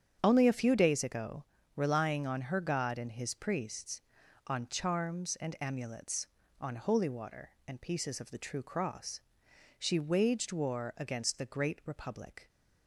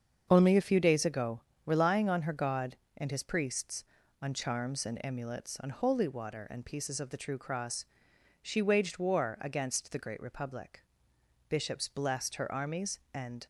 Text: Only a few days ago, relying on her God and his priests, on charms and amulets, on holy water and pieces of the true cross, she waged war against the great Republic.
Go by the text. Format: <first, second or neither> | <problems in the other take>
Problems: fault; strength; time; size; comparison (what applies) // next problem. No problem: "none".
first | starts louder than the rest; until 1.3 s; 7 dB; strong in the first // goes on to say "Bishops blessed her armies and"; strong; from 11.4 s on; 1.9 s long